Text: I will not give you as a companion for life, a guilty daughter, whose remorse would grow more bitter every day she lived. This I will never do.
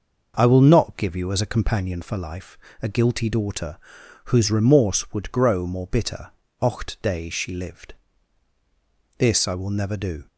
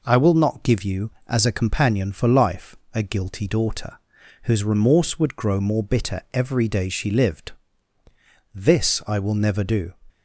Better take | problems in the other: second | says "ocht" for "every"; at 6.6 s

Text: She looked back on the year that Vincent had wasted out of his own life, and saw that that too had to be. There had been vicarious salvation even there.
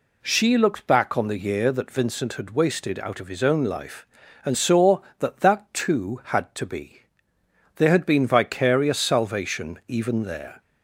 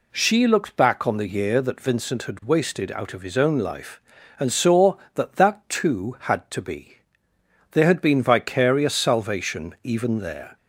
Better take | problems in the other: neither | none

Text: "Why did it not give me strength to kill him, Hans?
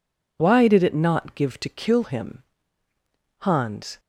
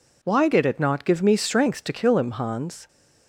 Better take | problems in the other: second | skips "me strength"; at 1.5 s

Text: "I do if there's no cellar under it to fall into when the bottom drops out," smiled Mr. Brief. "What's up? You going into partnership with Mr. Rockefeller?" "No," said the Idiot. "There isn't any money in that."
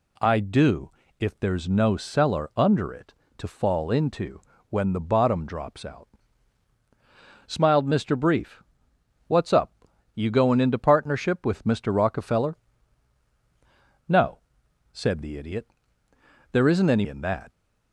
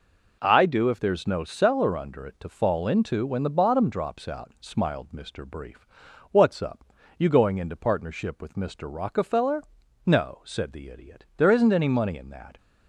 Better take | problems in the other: second | pauses between "do" and "if"; slight; at 0.9 s; 0.28 s long // pauses between "into" and "when"; slight; at 4.4 s; 0.30 s long // skips "money"; at 17.0 s

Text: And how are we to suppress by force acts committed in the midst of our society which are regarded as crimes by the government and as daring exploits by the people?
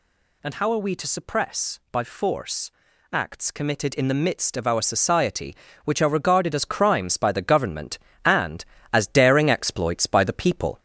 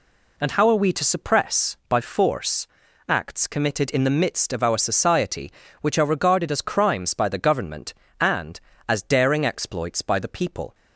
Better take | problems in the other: second | gets louder; slight; throughout; 2.5 dB // pauses between "force" and "acts"; at 2.7 s; 0.40 s long; also in the second

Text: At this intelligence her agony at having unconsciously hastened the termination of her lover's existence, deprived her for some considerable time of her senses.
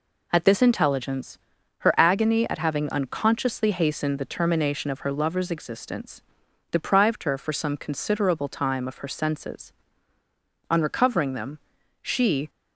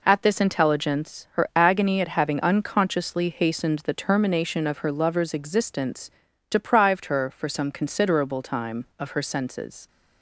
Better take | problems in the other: second | pauses between "intelligence" and "her"; noticeable; at 1.3 s; 0.46 s long // goes on to say "On recovering them she"; strong; from 10.6 s on; 1.8 s long

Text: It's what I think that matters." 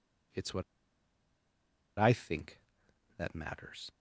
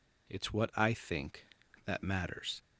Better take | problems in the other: second | pauses between "what" and "I"; strong; at 0.6 s; 1.3 s long

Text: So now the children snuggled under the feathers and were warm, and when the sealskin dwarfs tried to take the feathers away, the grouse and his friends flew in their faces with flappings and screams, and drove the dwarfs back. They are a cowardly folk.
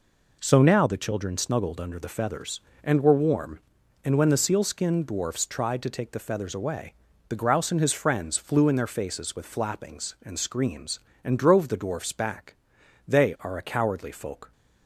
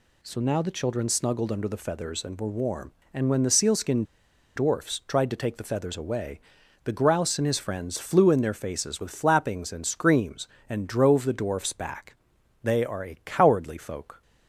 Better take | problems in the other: first | pauses between "sealskin" and "dwarfs"; noticeable; at 4.0 s; 0.52 s long

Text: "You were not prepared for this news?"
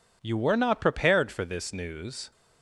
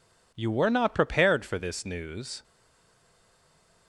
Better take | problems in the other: first | stays silent after the last word; noticeable; from 2.4 s on; 1.4 s long

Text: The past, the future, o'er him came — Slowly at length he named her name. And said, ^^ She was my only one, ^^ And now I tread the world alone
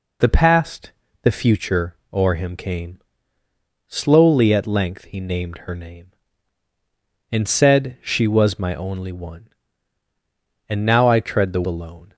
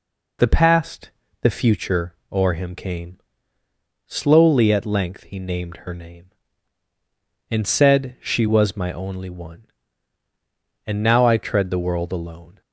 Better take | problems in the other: second | skips "world"; at 11.6 s

